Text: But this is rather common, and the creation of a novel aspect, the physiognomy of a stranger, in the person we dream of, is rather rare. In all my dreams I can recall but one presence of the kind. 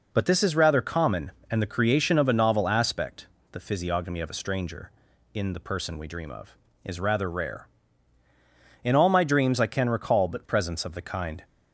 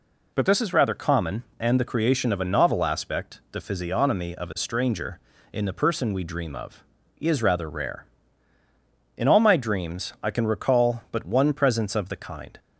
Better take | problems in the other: second | skips "one"; at 10.4 s

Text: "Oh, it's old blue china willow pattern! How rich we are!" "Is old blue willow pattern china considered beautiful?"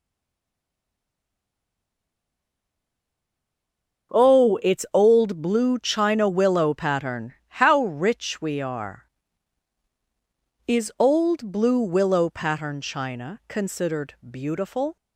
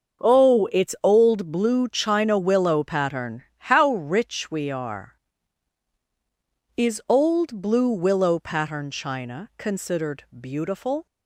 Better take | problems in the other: second | stays silent before the first word; strong; until 4.1 s; 4.1 s long // starts louder than the rest; until 5.2 s; 7 dB; also in the second

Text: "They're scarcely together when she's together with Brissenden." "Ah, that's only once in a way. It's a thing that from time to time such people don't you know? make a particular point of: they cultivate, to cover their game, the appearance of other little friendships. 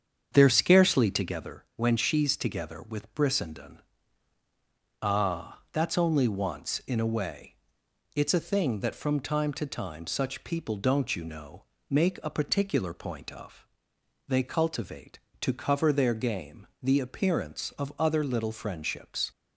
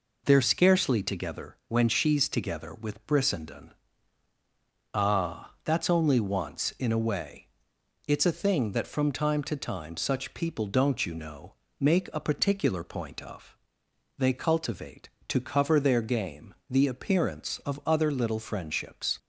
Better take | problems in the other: second | starts louder than the rest; strong; until 1.4 s; 7.5 dB

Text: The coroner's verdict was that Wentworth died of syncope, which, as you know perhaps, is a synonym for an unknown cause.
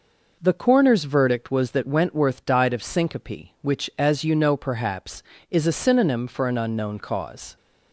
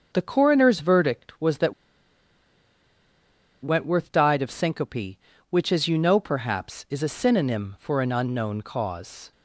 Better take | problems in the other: first | starts louder than the rest; until 1.1 s; 6.5 dB // pauses between "that" and "Wentworth"; strong; at 1.7 s; 1.8 s long

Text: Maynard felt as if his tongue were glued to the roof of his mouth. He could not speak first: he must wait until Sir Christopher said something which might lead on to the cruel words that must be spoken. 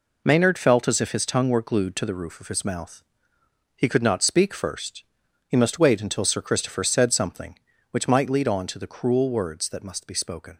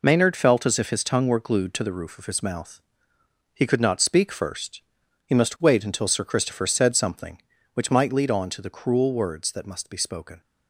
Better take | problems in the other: neither | none

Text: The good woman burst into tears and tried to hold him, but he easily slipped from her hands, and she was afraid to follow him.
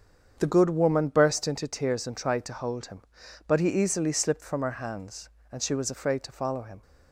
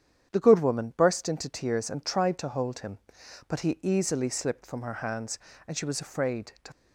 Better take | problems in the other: first | starts louder than the rest; strong; until 1.3 s; 9 dB; strong in the first // stops before "follow him"; at 6.7 s

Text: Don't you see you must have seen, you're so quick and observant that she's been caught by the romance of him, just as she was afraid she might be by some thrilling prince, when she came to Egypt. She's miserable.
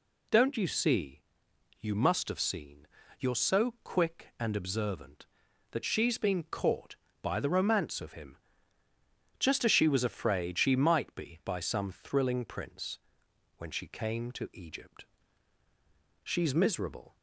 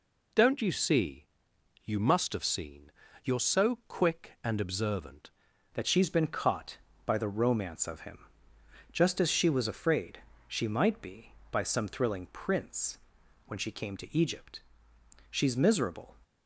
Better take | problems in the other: first | pauses between "see" and "you"; noticeable; at 1.2 s; 0.60 s long; noticeable in the first // changes voice at "that"; from 5.7 s on; 10.4 s long // pauses between "afraid" and "she"; slight; at 10.1 s; 0.28 s long

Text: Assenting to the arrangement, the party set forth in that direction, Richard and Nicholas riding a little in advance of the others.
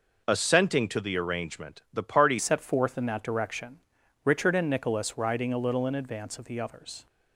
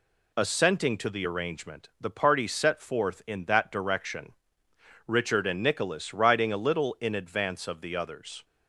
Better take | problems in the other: second | changes voice at "set"; from 2.3 s on; 4.7 s long

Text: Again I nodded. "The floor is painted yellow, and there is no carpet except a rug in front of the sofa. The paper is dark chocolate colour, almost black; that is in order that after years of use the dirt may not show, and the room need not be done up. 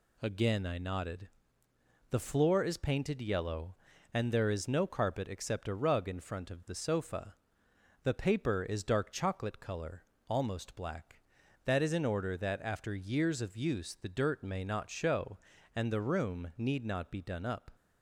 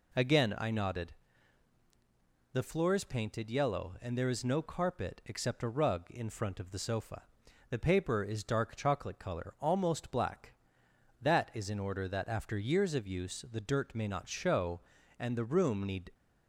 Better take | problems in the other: first | stops before "not be done up"; at 16.1 s

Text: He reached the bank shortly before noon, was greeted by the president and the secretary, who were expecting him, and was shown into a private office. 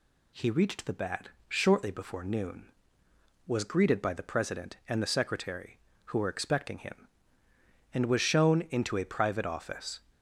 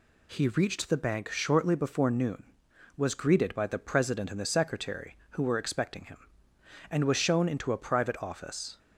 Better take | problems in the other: second | says "bat" for "bank"; at 0.9 s

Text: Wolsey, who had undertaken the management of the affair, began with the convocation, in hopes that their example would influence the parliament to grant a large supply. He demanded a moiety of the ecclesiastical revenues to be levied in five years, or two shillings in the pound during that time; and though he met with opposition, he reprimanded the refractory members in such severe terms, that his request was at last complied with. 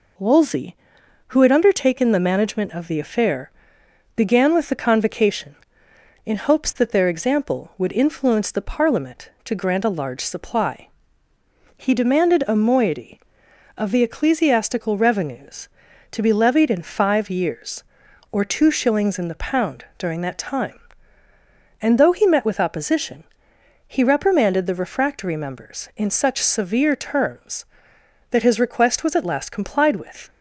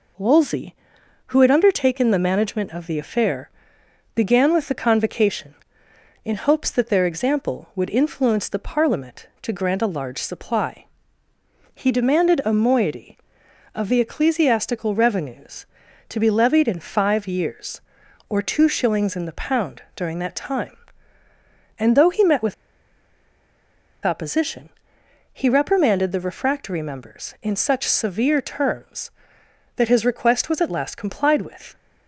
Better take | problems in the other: first | pauses between "with" and "opposition"; strong; at 22.5 s; 1.5 s long

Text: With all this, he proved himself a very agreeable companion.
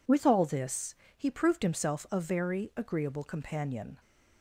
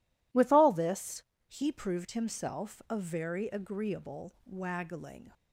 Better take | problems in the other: first | says "waggling" for "companion"; at 4.4 s

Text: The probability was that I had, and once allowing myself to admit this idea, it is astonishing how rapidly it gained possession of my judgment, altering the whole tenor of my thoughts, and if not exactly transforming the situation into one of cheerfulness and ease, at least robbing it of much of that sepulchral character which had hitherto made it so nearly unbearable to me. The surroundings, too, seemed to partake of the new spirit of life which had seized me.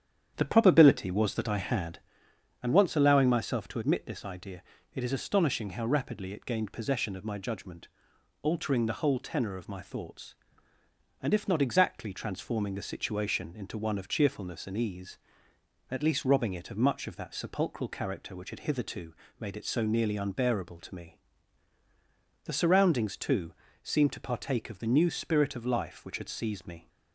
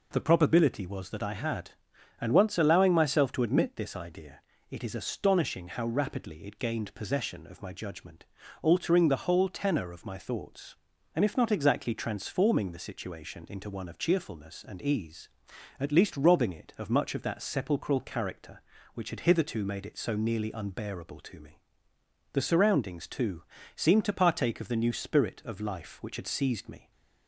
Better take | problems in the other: second | starts louder than the rest; strong; until 2.1 s; 9 dB // pauses between "hitherto" and "made"; slight; at 19.1 s; 0.26 s long

